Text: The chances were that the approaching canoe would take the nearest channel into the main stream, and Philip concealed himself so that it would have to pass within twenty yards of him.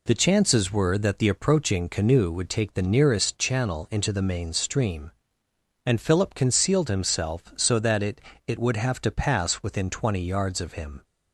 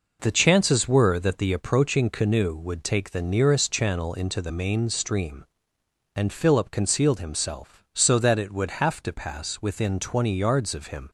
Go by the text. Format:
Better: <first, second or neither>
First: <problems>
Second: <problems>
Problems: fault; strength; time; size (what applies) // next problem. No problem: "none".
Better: second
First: says "it" twice; at 8.4 s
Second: none